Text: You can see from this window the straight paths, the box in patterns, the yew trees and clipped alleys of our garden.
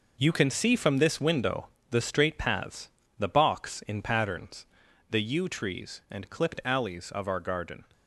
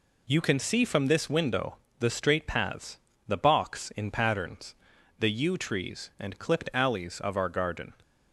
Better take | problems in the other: second | gets quieter; strong; throughout; 9.5 dB // pauses between "window" and "the"; slight; at 1.6 s; 0.24 s long; slight in the second

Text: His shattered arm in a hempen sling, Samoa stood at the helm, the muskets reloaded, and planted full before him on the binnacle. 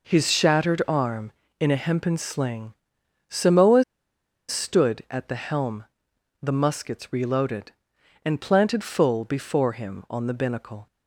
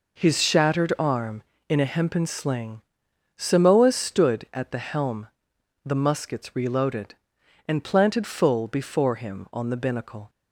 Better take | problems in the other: second | pauses between "Samoa" and "stood"; noticeable; at 3.8 s; 0.64 s long

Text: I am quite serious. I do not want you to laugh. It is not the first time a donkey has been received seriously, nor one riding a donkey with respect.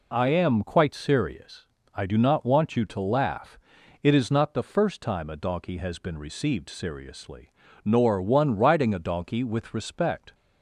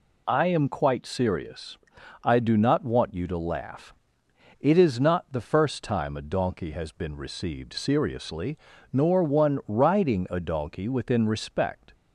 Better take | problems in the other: first | says "within" for "with"; at 10.8 s

